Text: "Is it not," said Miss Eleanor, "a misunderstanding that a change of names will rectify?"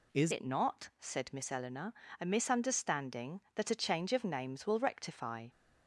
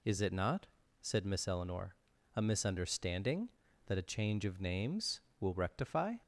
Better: second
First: changes voice at "it"; from 0.3 s on; 5.1 s long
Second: none

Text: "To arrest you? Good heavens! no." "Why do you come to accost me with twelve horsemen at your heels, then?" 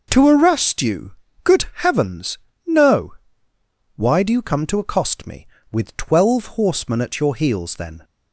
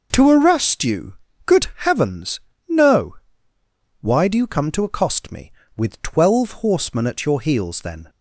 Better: neither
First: pauses between "Good" and "heavens"; slight; at 1.6 s; 0.18 s long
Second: pauses between "Good" and "heavens"; slight; at 1.6 s; 0.18 s long

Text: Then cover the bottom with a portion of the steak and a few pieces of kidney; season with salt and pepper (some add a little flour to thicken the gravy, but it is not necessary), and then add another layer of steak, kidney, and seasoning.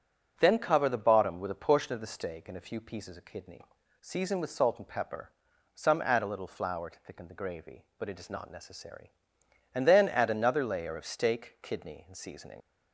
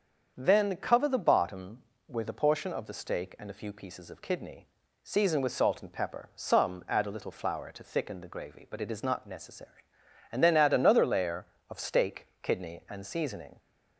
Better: second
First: starts louder than the rest; until 1.3 s; 6.5 dB // leaves "seasoning" unfinished; at 12.6 s; 80 ms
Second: starts louder than the rest; until 1.3 s; 7 dB

